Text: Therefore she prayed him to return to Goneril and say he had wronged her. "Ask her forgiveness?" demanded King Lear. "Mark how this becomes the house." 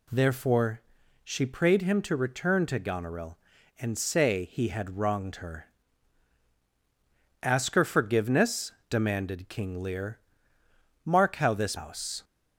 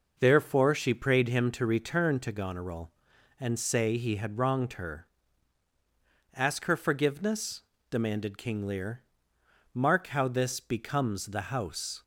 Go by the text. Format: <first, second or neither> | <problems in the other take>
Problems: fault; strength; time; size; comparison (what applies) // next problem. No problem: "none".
second | pauses between "Therefore" and "she"; at 0.8 s; 0.42 s long // skips "becomes the"; at 11.7 s